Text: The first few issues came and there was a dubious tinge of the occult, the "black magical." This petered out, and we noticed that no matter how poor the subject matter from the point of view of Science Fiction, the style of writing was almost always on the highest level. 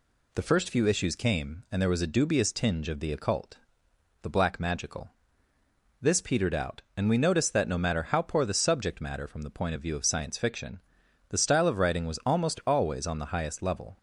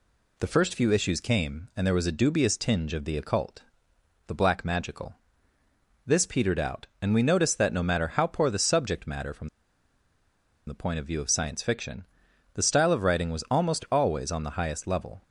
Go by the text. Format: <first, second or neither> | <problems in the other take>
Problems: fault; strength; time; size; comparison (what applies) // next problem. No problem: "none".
first | pauses between "from" and "the"; at 9.4 s; 1.1 s long